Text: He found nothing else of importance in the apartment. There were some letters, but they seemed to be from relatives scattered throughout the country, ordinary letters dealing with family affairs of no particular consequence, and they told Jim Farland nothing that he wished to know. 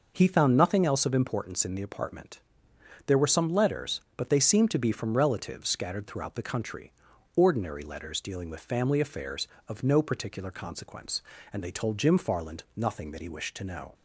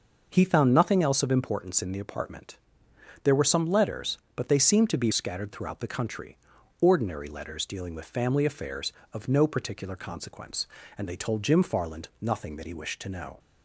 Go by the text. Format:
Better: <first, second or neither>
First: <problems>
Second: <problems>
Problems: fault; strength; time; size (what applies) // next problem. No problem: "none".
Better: first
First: none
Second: starts louder than the rest; noticeable; until 1.3 s; 6 dB // skips "from relatives"; at 5.1 s